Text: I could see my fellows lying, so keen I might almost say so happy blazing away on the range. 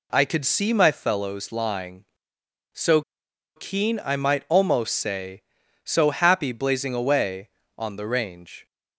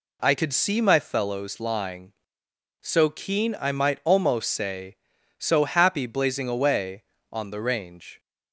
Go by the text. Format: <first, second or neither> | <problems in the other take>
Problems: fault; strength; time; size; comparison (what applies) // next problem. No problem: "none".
second | pauses between "so" and "keen"; noticeable; at 3.0 s; 0.55 s long